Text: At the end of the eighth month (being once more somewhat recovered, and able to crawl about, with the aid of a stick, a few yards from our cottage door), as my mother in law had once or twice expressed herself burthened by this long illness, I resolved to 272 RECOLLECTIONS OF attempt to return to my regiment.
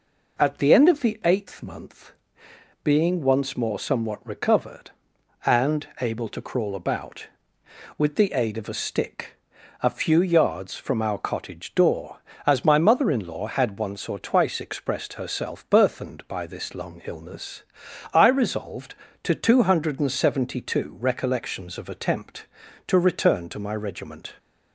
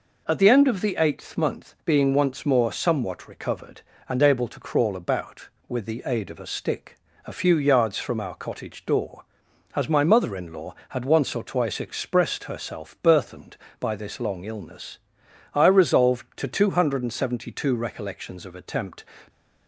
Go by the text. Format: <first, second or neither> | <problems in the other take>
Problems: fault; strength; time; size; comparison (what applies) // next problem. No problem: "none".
first | stops before "to return to my regiment"; at 19.2 s